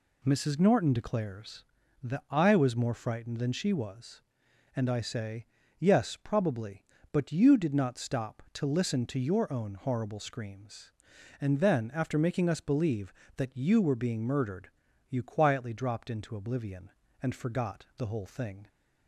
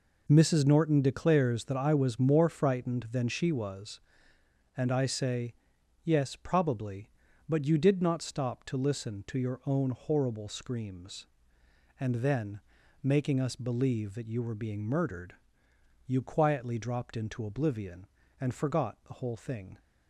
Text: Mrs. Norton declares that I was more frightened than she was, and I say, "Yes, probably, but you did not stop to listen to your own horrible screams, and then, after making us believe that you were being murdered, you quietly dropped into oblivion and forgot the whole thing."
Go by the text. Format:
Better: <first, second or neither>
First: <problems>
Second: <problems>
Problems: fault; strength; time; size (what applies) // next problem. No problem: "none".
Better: first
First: none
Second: skips "after"; at 12.8 s